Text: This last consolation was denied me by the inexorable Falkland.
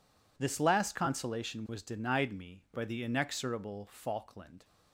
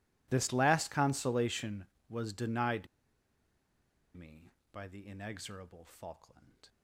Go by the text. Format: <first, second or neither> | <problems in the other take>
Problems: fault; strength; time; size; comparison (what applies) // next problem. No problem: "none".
first | pauses between "denied" and "me"; strong; at 2.8 s; 1.2 s long